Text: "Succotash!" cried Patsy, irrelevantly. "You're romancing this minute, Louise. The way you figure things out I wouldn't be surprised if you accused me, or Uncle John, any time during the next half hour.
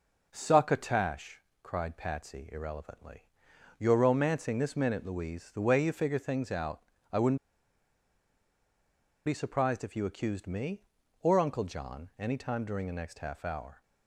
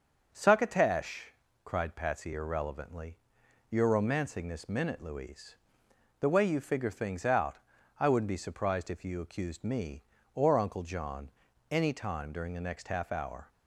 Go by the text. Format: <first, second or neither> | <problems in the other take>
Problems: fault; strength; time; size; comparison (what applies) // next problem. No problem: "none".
second | pauses between "out" and "I"; slight; at 6.8 s; 0.30 s long; also in the second // pauses between "wouldn't" and "be"; strong; at 7.3 s; 1.8 s long